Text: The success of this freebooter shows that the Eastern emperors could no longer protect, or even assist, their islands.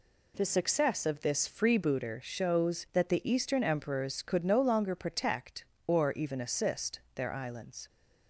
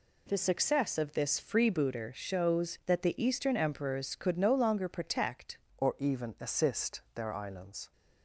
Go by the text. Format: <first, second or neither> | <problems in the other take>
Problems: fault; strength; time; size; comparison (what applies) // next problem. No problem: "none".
first | changes voice at "or"; from 5.7 s on; 2.2 s long